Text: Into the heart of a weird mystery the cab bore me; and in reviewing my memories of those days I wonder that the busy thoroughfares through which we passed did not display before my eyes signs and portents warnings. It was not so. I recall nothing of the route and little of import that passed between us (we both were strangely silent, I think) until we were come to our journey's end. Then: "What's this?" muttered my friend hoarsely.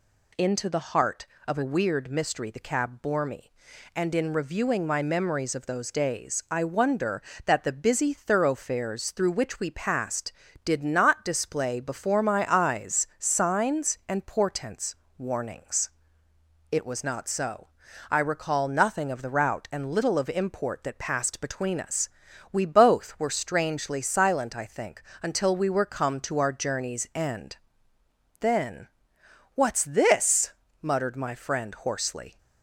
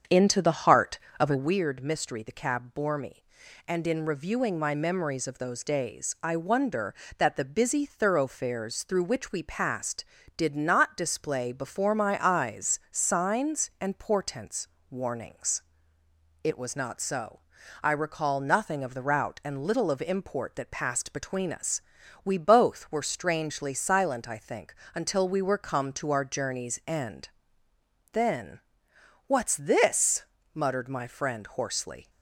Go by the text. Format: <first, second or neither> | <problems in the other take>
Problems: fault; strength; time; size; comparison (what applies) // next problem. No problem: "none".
first | starts louder than the rest; strong; until 1.5 s; 7.5 dB // pauses between "portents" and "warnings"; slight; at 14.6 s; 0.24 s long; slight in the first